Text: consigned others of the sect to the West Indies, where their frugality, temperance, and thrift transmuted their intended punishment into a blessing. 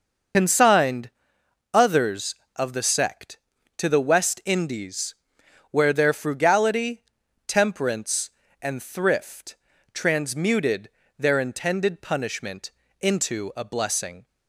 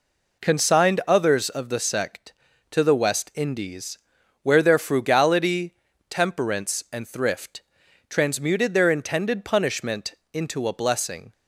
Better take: second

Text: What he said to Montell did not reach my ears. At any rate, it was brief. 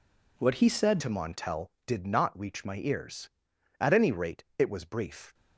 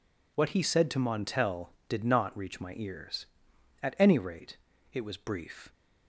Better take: second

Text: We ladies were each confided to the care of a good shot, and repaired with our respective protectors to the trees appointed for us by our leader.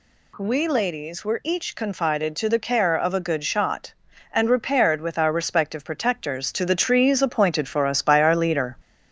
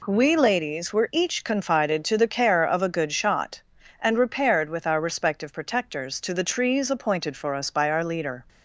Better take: second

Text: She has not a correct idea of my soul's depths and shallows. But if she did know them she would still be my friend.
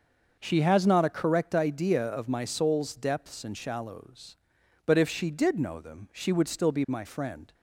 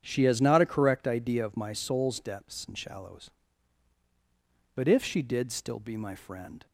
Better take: first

